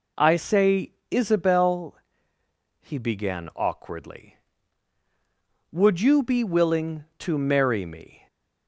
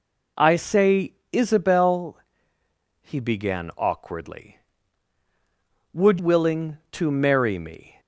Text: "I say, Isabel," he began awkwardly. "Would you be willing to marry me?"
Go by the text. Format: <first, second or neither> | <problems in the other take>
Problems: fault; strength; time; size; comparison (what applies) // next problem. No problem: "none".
first | skips "you be"; at 6.1 s